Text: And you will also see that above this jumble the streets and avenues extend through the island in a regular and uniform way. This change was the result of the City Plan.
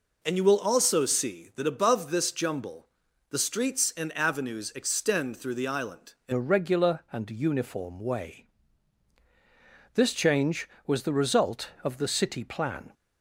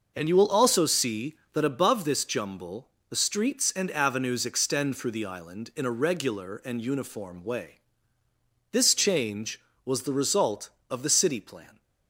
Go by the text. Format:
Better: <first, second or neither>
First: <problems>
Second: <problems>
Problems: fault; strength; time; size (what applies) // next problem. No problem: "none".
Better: second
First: pauses between "jumble" and "the"; at 2.8 s; 0.42 s long // changes voice at "a"; from 6.3 s on; 6.6 s long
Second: pauses between "jumble" and "the"; slight; at 2.8 s; 0.22 s long